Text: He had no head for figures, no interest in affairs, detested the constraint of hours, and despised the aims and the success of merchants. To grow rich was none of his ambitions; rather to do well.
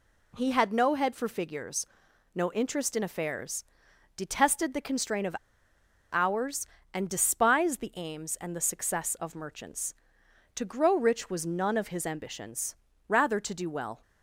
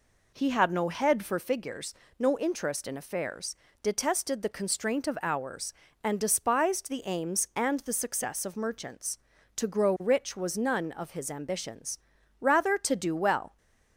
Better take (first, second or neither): second